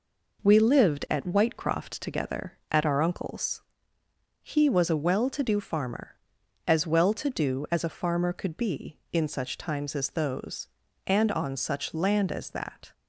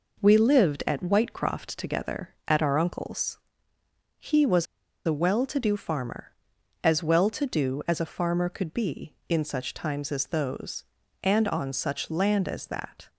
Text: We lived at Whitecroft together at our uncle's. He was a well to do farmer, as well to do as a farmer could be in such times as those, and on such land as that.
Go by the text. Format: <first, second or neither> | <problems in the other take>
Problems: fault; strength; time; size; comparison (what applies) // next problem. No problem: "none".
first | pauses between "was" and "a"; at 4.6 s; 0.39 s long